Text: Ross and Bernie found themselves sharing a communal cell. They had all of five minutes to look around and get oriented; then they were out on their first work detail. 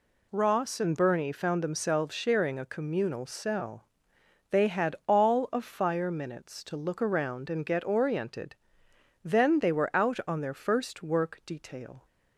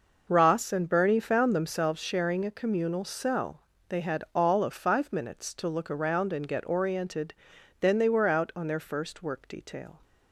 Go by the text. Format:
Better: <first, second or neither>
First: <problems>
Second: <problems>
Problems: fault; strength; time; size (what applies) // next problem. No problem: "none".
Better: second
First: says "fire" for "five"; at 5.6 s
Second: none